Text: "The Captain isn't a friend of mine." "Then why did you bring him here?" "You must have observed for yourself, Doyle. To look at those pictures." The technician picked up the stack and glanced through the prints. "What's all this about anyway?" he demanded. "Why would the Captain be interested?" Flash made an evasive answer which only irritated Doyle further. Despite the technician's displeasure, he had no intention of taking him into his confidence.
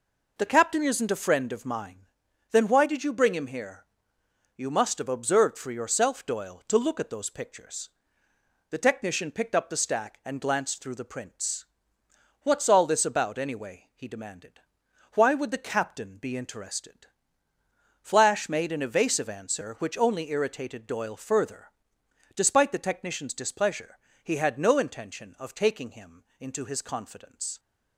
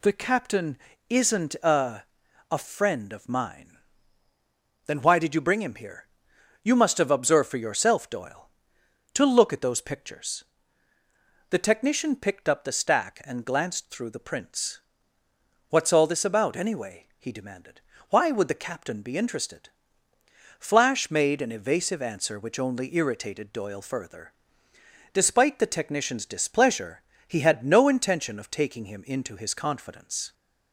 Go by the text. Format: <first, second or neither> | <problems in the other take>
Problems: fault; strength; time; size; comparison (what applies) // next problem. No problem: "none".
first | pauses between "Captain" and "isn't"; slight; at 0.7 s; 0.32 s long // says "a" twice; at 2.4 s